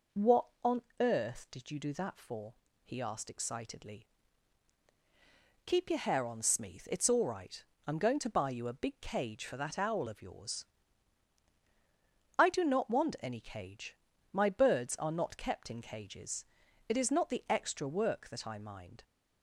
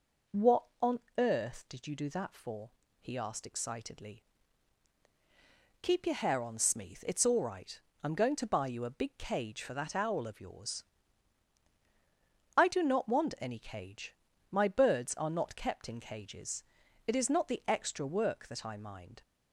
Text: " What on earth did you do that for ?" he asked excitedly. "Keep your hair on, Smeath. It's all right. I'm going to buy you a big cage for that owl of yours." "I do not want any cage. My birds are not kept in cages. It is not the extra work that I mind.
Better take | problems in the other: neither | pauses between "on" and "earth"; slight; the same in both

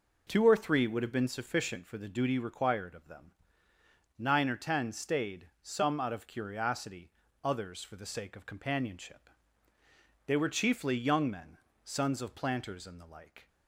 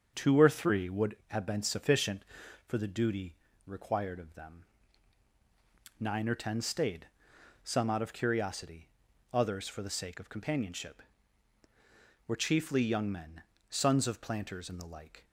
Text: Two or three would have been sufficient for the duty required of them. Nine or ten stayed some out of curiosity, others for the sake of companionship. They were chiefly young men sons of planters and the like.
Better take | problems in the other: first | starts louder than the rest; until 1.1 s; 7 dB // pauses between "duty" and "required"; slight; at 3.3 s; 0.32 s long // pauses between "stayed" and "some"; noticeable; at 7.0 s; 0.60 s long; slight in the first // skips "They"; at 11.6 s // pauses between "men" and "sons"; slight; at 13.4 s; 0.28 s long; slight in the first

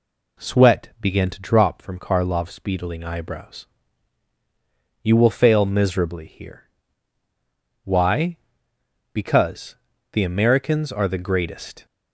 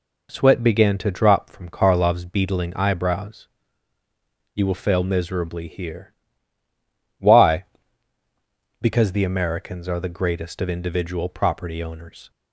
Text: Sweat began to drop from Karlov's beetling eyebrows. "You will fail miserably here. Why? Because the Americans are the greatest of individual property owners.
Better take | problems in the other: second | pauses between "Because" and "the"; slight; at 9.7 s; 0.34 s long // stops before "of individual property owners"; at 11.8 s

